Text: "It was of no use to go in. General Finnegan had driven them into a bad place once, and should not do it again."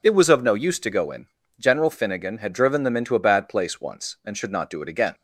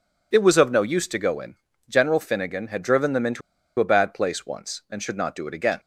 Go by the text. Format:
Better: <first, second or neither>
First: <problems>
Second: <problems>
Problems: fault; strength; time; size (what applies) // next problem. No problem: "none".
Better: first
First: none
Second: pauses between "into" and "a"; at 3.4 s; 0.38 s long